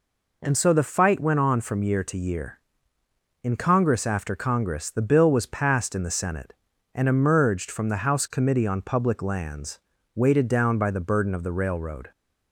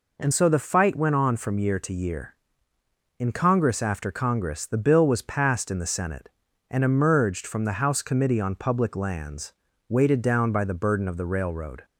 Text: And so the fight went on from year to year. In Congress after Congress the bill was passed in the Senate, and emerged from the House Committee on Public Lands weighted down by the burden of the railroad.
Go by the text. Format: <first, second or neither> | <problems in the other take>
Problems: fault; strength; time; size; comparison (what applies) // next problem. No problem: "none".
neither | pauses between "Lands" and "weighted"; slight; the same in both